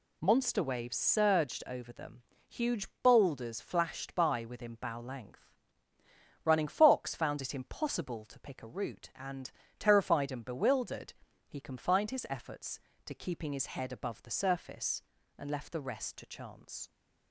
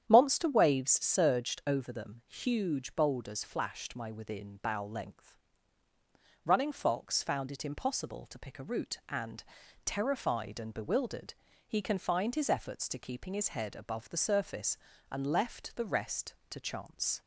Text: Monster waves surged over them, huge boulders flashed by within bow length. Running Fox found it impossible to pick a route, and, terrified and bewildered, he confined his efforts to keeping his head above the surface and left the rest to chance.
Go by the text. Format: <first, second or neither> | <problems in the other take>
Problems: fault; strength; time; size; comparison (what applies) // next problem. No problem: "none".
first | starts louder than the rest; strong; until 1.0 s; 9.5 dB // says "my" for "by"; at 3.9 s